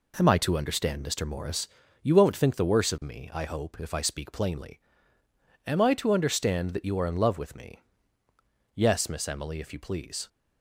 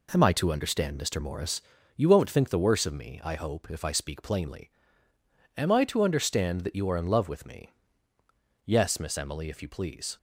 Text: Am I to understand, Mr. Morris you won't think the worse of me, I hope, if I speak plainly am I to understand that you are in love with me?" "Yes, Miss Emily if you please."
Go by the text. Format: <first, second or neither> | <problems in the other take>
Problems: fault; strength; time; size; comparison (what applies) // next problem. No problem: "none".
neither | pauses between "Morris" and "you"; slight; the same in both // pauses between "plainly" and "am"; noticeable; the same in both